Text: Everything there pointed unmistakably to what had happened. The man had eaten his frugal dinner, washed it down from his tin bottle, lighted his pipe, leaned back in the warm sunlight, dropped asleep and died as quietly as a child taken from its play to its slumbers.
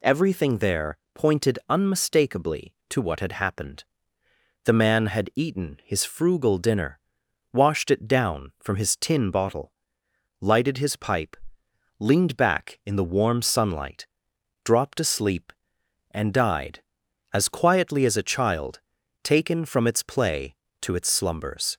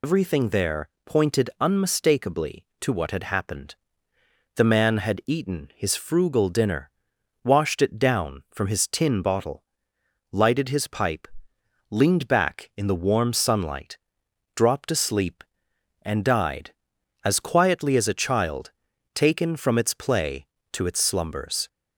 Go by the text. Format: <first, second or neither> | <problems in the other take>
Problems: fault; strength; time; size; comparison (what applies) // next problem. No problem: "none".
first | loses the start of "Everything"; at 0.0 s; 100 ms // pauses between "there" and "pointed"; slight; at 0.8 s; 0.18 s long; slight in the first // pauses between "child" and "taken"; at 18.7 s; 0.42 s long; also in the first